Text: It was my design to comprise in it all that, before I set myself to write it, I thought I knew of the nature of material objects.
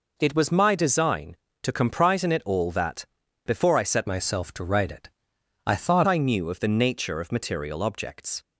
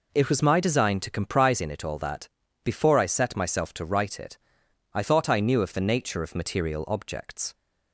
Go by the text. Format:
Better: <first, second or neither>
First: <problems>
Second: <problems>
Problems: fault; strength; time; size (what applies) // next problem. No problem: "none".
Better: second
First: changes voice from "myself" to "thought"; from 4.0 to 6.0 s; 2.0 s long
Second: none